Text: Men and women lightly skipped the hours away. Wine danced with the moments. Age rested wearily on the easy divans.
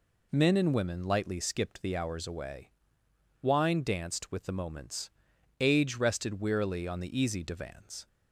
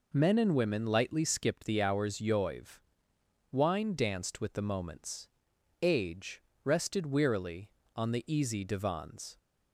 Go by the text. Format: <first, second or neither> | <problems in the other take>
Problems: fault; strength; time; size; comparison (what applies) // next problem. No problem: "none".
first | says "yoiv" for "away"; at 2.1 s // pauses between "Age" and "rested"; slight; at 6.4 s; 0.22 s long